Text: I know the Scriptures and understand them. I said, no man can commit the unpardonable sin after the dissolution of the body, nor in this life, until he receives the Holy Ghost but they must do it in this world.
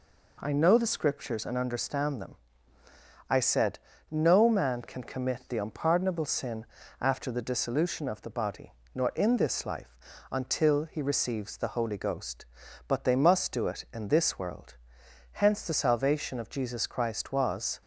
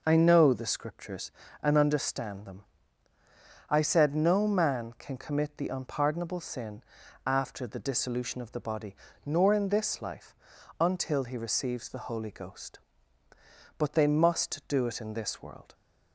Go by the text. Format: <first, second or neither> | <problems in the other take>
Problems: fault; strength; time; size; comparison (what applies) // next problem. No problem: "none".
second | pauses between "sin" and "after"; slight; at 6.6 s; 0.34 s long; also in the second // goes on to say "Hence the salvation of Jesus Christ was"; strong; from 15.3 s on; 2.4 s long